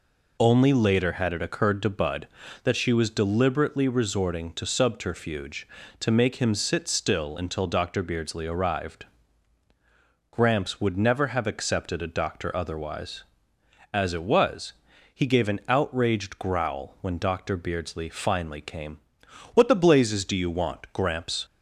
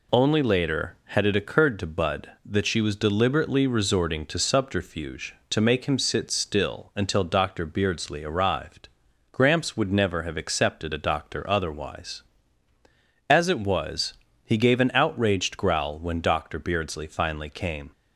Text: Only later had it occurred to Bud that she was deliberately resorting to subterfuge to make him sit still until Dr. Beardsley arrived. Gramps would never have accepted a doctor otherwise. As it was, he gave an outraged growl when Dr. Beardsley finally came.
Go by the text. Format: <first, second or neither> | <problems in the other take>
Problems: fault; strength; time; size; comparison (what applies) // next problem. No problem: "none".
second | goes on to say "What the blazes do you want Gramps"; strong; from 19.5 s on; 1.9 s long